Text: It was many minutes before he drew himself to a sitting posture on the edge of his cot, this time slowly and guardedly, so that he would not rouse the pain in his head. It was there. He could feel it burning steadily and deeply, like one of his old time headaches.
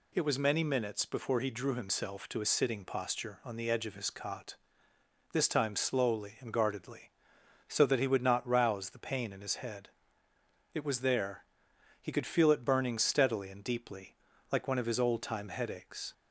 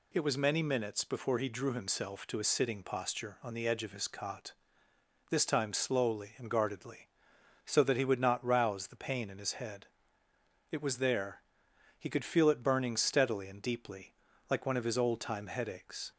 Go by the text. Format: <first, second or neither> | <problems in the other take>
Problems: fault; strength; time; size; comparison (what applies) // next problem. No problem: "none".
neither | none